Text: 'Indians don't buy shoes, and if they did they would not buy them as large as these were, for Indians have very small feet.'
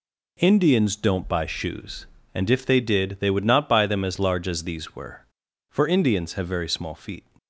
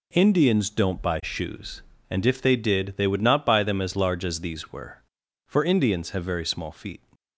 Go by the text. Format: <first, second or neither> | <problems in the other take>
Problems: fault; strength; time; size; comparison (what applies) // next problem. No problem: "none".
neither | none